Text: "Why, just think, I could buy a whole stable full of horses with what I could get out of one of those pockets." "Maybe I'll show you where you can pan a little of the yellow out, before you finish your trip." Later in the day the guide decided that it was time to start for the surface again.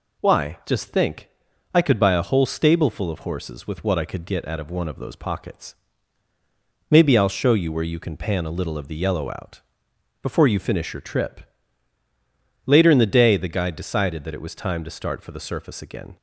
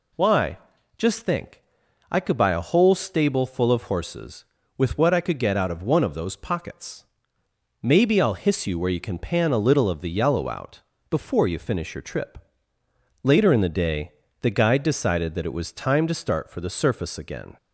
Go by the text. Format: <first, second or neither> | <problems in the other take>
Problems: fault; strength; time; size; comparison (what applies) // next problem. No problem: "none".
first | says "hiss" for "show"; at 8.3 s // pauses between "day" and "the"; slight; at 14.1 s; 0.30 s long